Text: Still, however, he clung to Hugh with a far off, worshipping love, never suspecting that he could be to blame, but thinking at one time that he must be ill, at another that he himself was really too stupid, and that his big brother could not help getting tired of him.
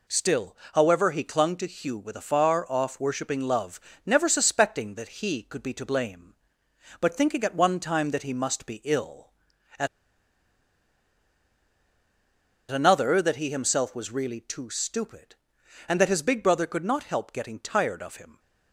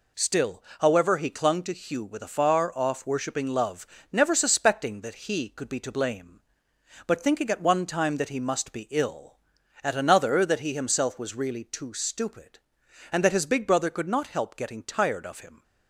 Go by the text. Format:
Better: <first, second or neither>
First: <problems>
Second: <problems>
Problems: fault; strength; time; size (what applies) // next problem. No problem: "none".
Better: second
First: pauses between "at" and "another"; strong; at 9.8 s; 2.8 s long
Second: none